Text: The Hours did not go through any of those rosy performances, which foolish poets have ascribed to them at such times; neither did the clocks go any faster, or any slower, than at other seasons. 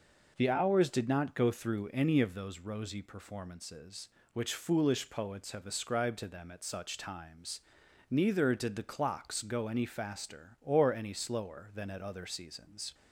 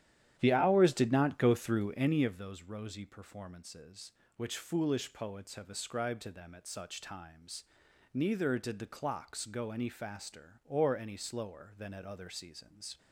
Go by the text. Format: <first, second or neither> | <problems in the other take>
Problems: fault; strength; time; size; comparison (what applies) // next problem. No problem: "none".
first | starts louder than the rest; strong; until 2.3 s; 11 dB